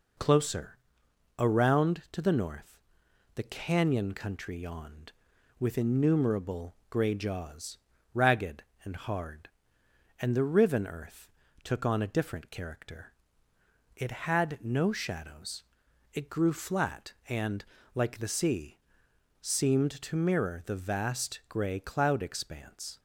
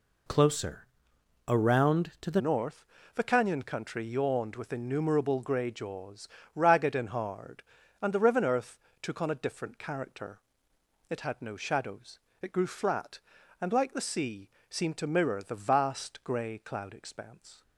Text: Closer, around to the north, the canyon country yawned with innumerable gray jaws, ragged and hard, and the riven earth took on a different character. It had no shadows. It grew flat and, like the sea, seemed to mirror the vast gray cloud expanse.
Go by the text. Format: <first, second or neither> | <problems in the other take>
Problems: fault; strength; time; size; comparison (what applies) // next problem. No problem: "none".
first | changes voice at "north"; from 2.3 s on; 15.3 s long // pauses between "earth" and "took"; slight; at 8.7 s; 0.24 s long; slight in the first